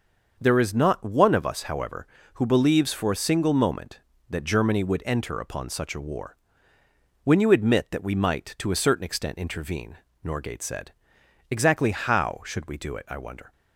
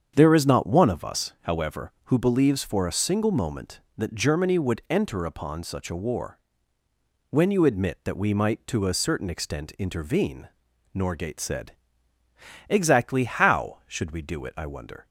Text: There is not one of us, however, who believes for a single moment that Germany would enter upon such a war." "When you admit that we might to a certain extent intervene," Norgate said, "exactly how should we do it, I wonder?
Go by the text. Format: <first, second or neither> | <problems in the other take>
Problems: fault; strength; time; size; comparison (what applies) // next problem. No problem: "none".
neither | starts louder than the rest; the same in both